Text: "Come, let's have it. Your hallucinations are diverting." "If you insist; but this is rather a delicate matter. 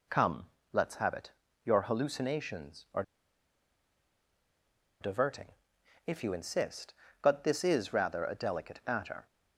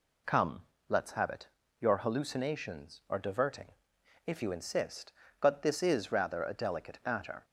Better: second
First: pauses between "are" and "diverting"; strong; at 3.0 s; 1.9 s long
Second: none

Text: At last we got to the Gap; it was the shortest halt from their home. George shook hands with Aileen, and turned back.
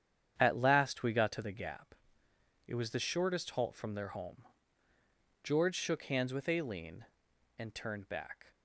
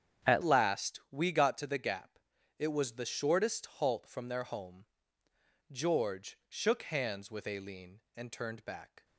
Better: first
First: starts louder than the rest; strong; until 1.3 s; 9 dB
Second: starts louder than the rest; strong; until 1.3 s; 9 dB // changes voice at "last"; from 0.4 s on; 8.6 s long

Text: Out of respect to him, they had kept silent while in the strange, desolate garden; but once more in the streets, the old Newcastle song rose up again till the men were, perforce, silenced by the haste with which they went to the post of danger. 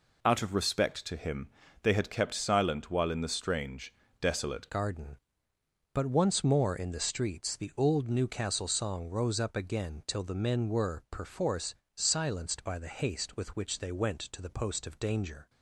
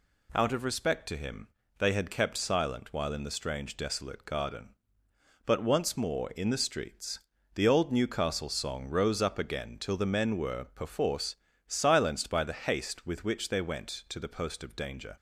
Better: second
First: changes voice at "garden"; from 4.6 s on; 10.8 s long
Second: none

